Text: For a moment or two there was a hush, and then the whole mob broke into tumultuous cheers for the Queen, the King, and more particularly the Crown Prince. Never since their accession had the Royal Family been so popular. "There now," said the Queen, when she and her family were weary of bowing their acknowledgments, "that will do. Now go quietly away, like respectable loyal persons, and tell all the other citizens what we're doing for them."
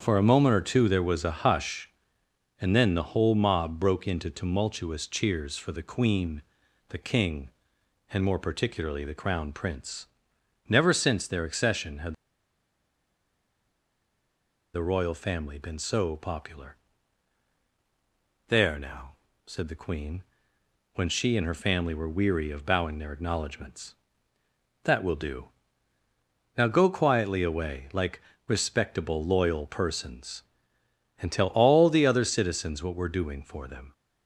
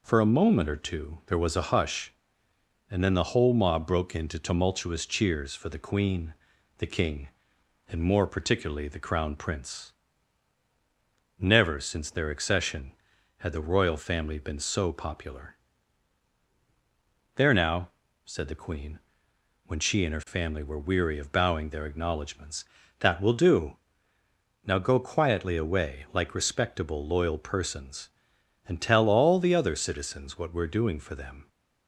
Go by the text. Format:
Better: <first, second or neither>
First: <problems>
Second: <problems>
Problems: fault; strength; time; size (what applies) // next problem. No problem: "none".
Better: second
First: starts louder than the rest; strong; until 1.0 s; 7.5 dB // pauses between "had" and "the"; strong; at 12.1 s; 2.5 s long // pauses between "like" and "respectable"; slight; at 28.2 s; 0.26 s long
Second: none